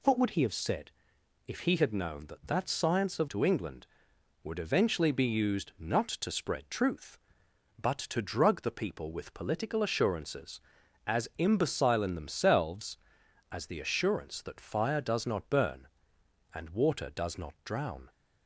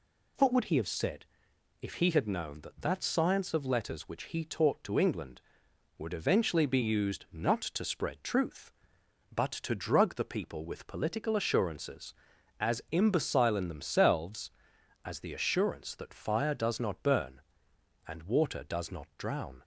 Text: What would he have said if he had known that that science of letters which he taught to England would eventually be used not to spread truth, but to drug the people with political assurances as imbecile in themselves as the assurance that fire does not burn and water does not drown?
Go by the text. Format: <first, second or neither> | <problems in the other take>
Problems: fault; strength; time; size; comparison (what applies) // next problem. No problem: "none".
second | pauses between "said" and "if"; noticeable; at 0.9 s; 0.56 s long; noticeable in the second // skips "letters which he taught"; at 3.2 s